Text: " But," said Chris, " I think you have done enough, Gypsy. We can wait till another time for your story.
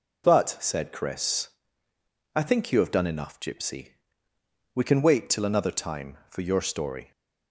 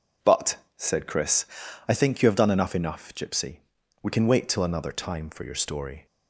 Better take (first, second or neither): first